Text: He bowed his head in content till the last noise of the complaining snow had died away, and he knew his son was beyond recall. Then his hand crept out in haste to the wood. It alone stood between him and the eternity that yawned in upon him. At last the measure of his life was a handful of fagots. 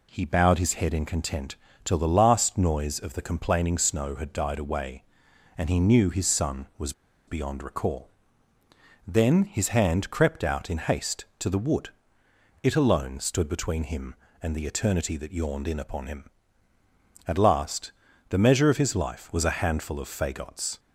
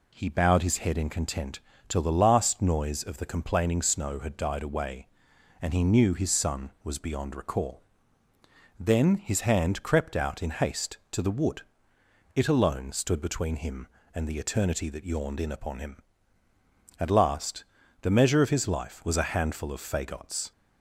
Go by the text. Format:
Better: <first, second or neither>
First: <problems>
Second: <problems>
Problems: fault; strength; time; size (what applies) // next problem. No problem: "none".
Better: second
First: pauses between "content" and "till"; slight; at 1.5 s; 0.28 s long // pauses between "was" and "beyond"; slight; at 6.9 s; 0.35 s long // pauses between "last" and "the"; slight; at 17.9 s; 0.36 s long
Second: pauses between "content" and "till"; slight; at 1.5 s; 0.28 s long // pauses between "last" and "the"; slight; at 17.6 s; 0.36 s long